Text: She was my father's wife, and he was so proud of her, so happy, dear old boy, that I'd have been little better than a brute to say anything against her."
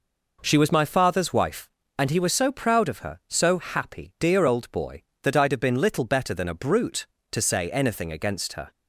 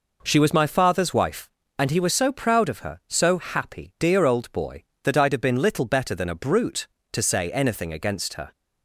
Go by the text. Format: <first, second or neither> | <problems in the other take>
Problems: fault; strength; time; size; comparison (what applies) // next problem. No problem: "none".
neither | none